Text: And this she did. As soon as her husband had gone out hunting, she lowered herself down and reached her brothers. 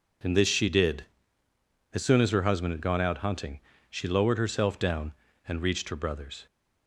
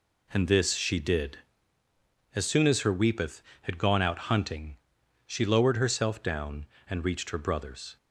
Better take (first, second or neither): first